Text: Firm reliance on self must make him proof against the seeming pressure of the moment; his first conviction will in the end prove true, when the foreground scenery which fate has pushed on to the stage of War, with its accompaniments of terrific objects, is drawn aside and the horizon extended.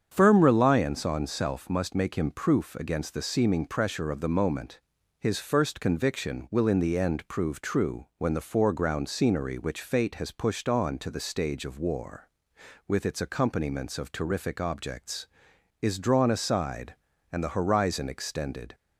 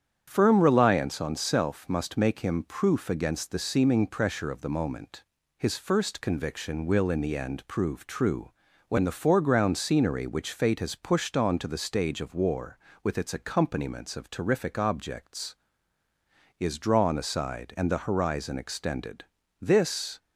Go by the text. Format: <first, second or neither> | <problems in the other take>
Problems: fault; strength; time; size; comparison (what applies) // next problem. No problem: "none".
first | starts louder than the rest; strong; until 1.2 s; 8.5 dB; strong in the first // goes on to say "This"; from 19.6 s on; 0.56 s long